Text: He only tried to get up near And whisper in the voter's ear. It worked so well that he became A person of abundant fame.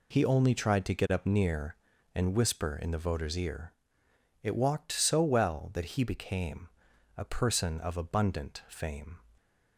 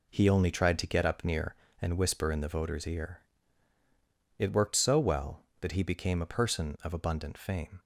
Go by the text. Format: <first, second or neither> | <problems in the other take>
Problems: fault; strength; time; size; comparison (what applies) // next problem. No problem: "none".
second | says "walked" for "worked"; at 4.5 s // pauses between "became" and "A"; noticeable; at 6.6 s; 0.48 s long